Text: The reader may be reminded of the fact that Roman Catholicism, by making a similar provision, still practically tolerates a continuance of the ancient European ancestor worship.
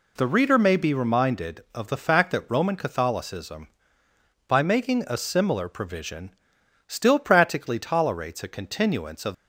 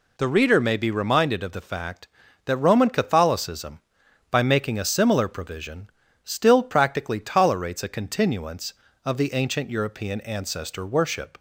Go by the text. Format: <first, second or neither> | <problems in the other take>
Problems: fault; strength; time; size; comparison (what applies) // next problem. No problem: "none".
second | stops before "the ancient European ancestor worship"; at 9.3 s